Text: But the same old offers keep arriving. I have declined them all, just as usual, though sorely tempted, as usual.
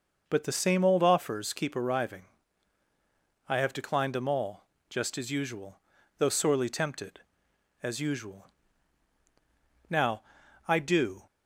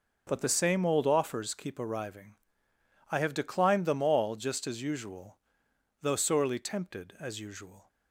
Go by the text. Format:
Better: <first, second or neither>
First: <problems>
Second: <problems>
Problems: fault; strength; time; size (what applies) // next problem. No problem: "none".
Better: second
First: goes on to say "Now I do"; from 9.8 s on; 1.3 s long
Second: none